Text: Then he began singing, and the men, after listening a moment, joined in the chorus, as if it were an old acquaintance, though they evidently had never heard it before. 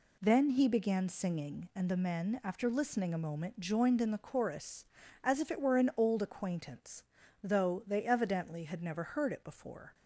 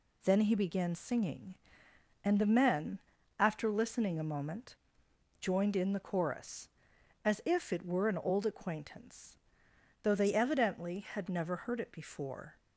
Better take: neither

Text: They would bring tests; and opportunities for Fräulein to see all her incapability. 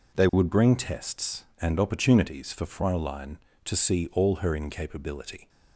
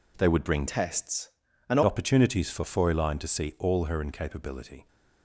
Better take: first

